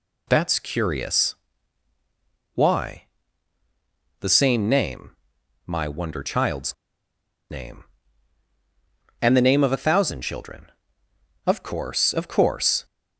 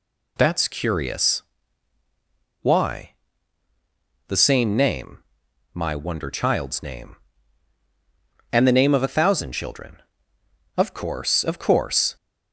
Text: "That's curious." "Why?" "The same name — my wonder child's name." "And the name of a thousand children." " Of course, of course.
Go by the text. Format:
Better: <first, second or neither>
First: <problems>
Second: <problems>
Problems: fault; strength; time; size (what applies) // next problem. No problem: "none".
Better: second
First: pauses between "child's" and "name"; noticeable; at 6.7 s; 0.76 s long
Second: none